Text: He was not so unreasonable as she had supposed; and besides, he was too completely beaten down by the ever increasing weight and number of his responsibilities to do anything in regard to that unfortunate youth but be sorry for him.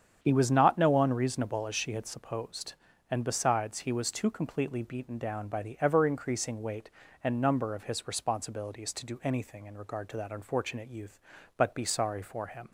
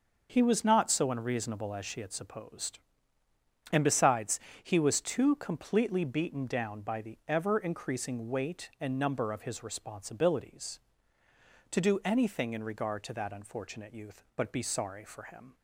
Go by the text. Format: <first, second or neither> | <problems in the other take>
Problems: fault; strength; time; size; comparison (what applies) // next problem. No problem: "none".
second | starts louder than the rest; strong; until 1.2 s; 8 dB; also in the second // says "no" for "so"; at 0.7 s